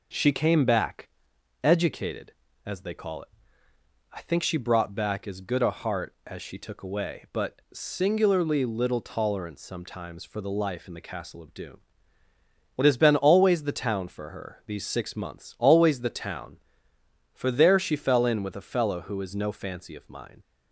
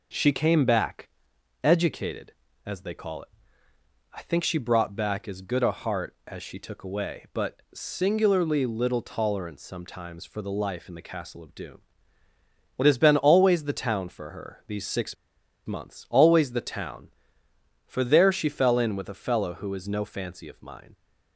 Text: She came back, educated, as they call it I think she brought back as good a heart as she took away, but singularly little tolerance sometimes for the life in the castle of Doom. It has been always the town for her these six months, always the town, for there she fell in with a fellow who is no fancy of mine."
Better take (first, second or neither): first